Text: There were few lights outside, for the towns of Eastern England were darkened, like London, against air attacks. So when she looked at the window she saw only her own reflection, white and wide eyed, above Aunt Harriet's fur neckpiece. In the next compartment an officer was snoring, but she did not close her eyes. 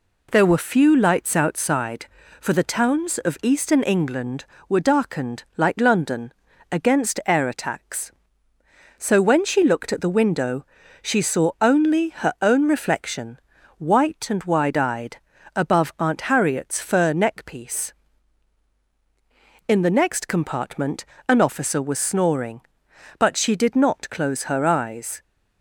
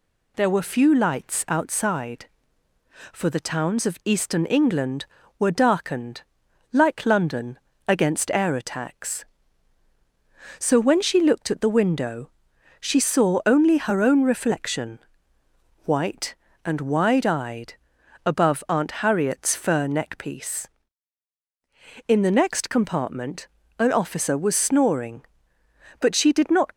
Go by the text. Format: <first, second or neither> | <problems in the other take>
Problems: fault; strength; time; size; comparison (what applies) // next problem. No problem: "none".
first | pauses between "window" and "she"; noticeable; at 12.2 s; 0.50 s long; slight in the first // pauses between "compartment" and "an"; slight; at 23.4 s; 0.30 s long; slight in the first // stops before "close her eyes"; at 26.7 s